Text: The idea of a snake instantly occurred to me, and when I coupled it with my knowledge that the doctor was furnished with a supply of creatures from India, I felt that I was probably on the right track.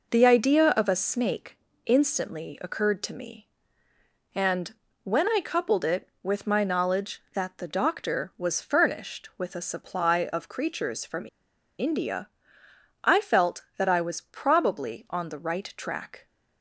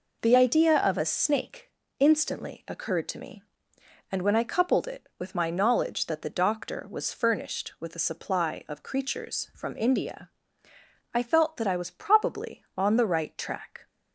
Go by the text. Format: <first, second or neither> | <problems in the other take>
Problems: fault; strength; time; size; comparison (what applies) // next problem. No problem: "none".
second | pauses between "snake" and "instantly"; slight; at 1.5 s; 0.26 s long; slight in the second // pauses between "and" and "when"; slight; at 4.7 s; 0.30 s long // pauses between "from" and "India"; noticeable; at 11.2 s; 0.52 s long